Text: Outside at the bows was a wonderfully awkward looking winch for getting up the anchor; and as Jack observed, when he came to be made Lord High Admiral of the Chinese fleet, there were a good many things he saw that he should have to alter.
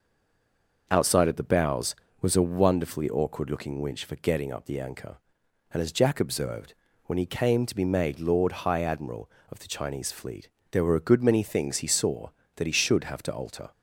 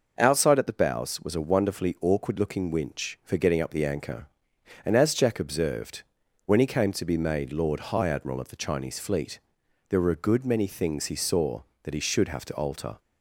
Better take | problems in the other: second | stays silent before the first word; slight; until 0.8 s; 0.8 s long

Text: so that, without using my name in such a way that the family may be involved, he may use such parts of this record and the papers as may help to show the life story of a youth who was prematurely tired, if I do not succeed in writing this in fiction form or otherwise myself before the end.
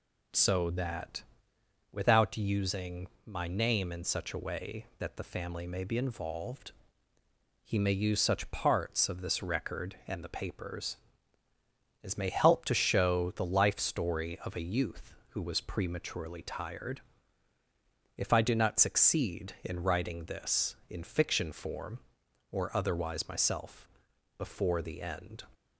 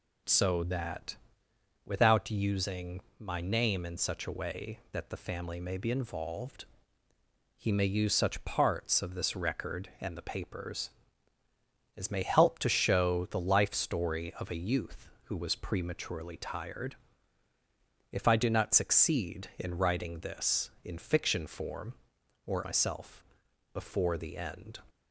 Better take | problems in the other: first | pauses between "using" and "my"; slight; at 2.9 s; 0.18 s long; slight in the first // skips "otherwise"; at 22.6 s // pauses between "myself" and "before"; noticeable; at 23.2 s; 0.50 s long; noticeable in the first

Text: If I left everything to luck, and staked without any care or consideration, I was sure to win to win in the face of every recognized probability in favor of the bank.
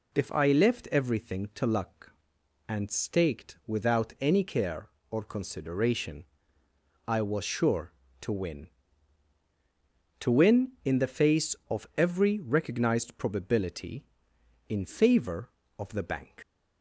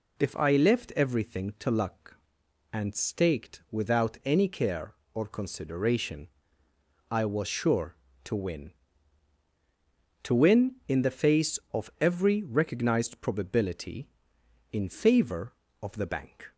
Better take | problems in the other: second | leaves "bank" unfinished; at 16.4 s; 85 ms

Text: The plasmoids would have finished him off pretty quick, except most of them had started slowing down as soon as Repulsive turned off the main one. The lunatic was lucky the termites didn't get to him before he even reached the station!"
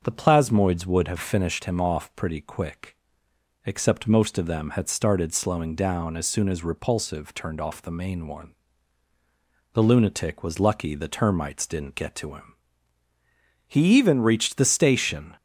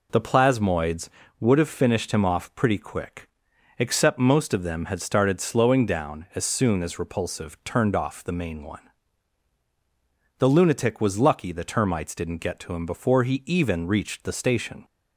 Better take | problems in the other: second | starts louder than the rest; until 1.0 s; 6.5 dB // skips "before"; at 13.1 s

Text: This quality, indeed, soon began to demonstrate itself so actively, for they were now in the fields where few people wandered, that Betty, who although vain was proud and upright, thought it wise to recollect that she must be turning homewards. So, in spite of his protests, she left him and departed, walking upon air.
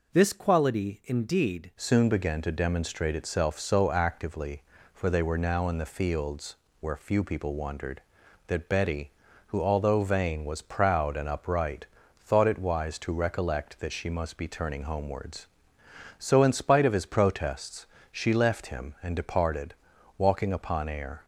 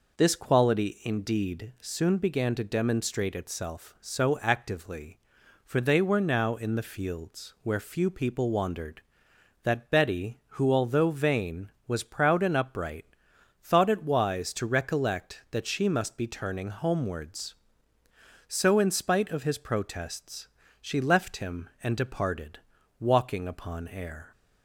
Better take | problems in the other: second | changes voice at "soon"; from 1.7 s on; 19.5 s long // pauses between "fields" and "where"; slight; at 6.5 s; 0.24 s long

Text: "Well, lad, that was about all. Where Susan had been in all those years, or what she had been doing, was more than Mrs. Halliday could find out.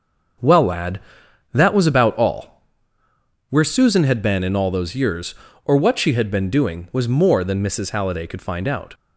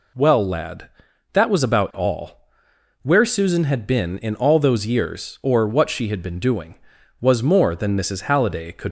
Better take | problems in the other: first | stops before "find out"; at 8.8 s

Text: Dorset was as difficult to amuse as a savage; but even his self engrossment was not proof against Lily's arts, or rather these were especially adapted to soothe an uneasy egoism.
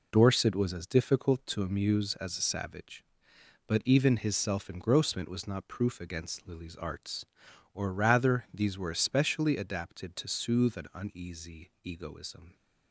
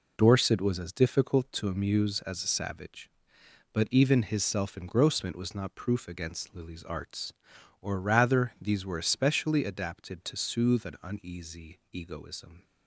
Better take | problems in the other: neither | none

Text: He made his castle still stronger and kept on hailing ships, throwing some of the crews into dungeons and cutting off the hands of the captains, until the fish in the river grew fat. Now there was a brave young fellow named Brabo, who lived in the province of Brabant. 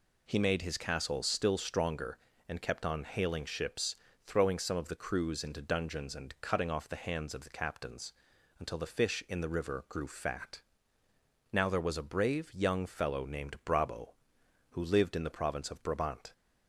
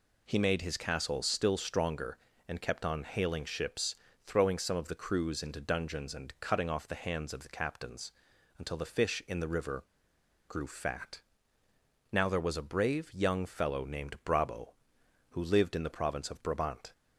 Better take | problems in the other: first | pauses between "river" and "grew"; noticeable; at 9.8 s; 0.63 s long

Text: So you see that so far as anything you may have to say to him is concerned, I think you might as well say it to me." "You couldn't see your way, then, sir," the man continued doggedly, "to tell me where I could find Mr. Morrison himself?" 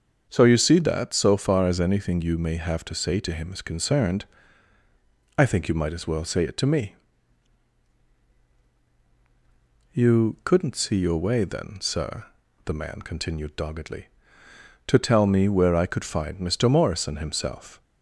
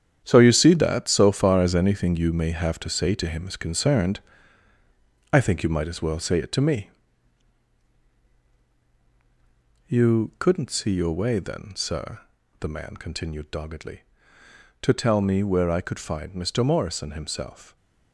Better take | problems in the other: first | gets quieter; strong; throughout; 10 dB // starts louder than the rest; strong; until 1.2 s; 9 dB; also in the first

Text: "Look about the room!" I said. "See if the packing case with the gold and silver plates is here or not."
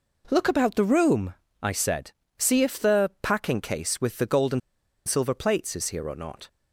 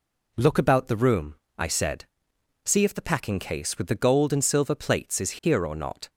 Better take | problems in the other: second | pauses between "and" and "silver"; noticeable; at 4.6 s; 0.47 s long

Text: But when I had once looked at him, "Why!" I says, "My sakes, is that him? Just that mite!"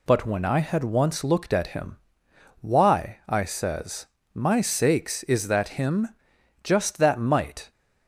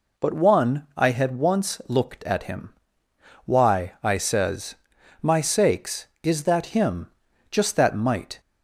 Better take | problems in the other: first | says "one" for "when"; at 0.3 s

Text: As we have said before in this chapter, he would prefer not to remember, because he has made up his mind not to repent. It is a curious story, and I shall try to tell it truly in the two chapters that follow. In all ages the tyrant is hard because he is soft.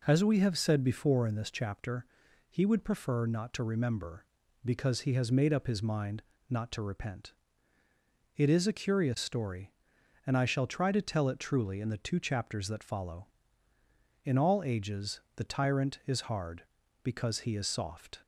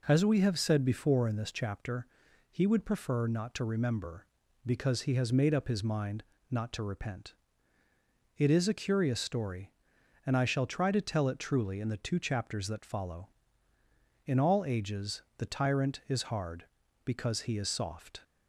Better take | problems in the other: neither | pauses between "mind" and "not"; slight; the same in both // pauses between "ages" and "the"; slight; the same in both

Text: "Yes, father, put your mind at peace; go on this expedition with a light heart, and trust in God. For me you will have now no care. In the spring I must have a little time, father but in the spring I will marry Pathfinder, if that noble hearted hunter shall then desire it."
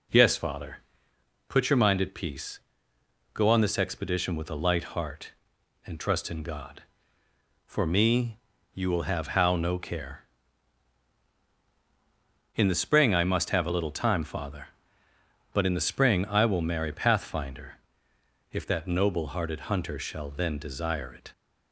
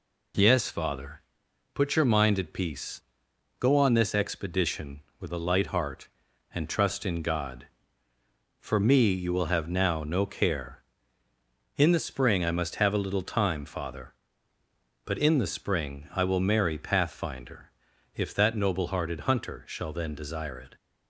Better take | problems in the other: second | pauses between "me" and "you"; slight; at 8.3 s; 0.36 s long // says "how" for "now"; at 9.3 s

